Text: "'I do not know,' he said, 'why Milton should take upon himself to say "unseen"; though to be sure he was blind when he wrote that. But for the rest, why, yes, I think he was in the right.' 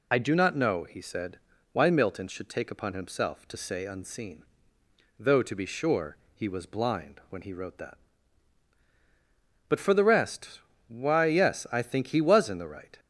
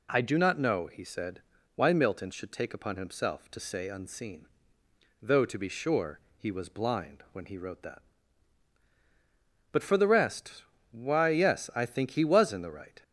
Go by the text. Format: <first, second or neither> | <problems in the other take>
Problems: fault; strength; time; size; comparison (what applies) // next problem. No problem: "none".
second | loses the start of "I"; at 0.1 s; 55 ms // pauses between "sure" and "he"; slight; at 6.1 s; 0.18 s long; slight in the second